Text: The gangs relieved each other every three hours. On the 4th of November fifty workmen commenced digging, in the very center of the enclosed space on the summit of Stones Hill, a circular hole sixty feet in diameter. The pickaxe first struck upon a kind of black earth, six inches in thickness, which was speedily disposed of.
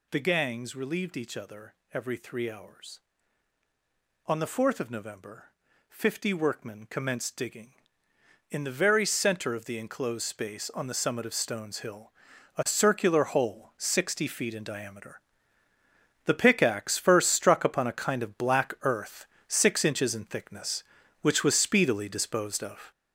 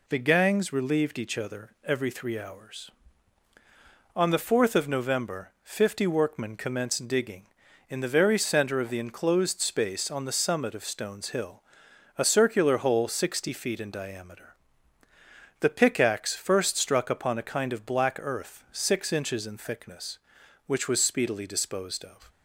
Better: second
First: gets louder; throughout; 7 dB // pauses between "other" and "every"; slight; at 1.7 s; 0.18 s long // pauses between "November" and "fifty"; at 5.5 s; 0.40 s long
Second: none

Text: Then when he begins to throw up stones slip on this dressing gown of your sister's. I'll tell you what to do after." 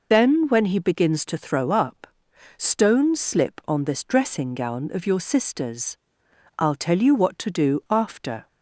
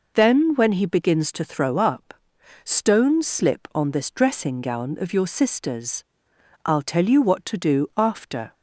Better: second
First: loses the start of "Then"; at 0.1 s; 25 ms // pauses between "up" and "stones"; noticeable; at 2.0 s; 0.52 s long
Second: pauses between "up" and "stones"; noticeable; at 2.1 s; 0.52 s long

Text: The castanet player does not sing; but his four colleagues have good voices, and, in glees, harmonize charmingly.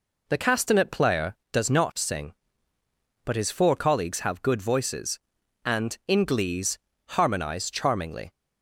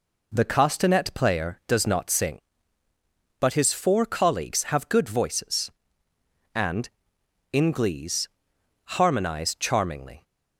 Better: neither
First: none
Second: none

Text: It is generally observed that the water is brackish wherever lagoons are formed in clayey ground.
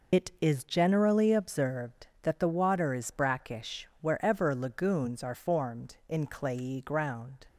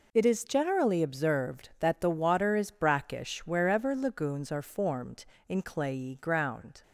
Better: second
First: loses the start of "It"; at 0.1 s; 115 ms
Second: none

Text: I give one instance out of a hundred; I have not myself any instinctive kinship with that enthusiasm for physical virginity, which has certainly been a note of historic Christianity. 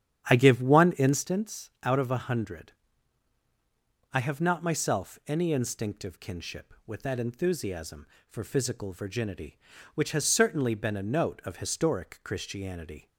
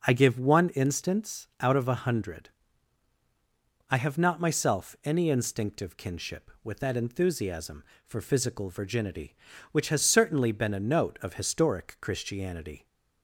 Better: second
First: starts louder than the rest; strong; until 1.3 s; 9 dB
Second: none

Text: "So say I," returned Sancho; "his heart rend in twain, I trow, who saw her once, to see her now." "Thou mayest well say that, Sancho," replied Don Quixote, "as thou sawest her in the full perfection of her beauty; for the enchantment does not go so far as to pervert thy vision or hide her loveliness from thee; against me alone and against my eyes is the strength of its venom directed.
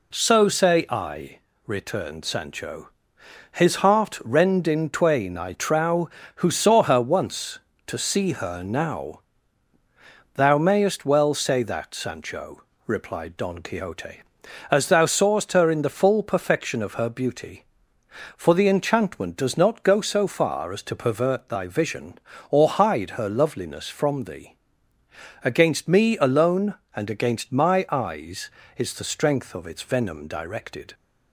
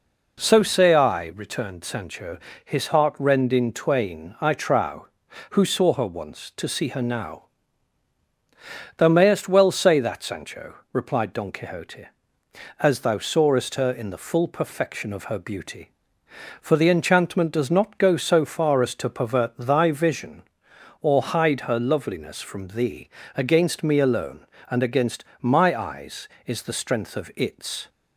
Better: first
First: none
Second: pauses between "against" and "my"; slight; at 25.2 s; 0.16 s long // stops before "venom directed"; at 27.8 s

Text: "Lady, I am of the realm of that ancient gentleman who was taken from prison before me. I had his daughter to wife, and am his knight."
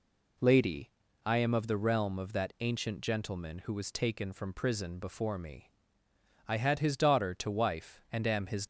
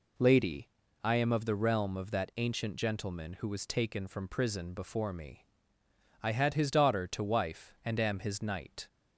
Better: second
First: stops before "knight"; at 8.6 s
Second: none

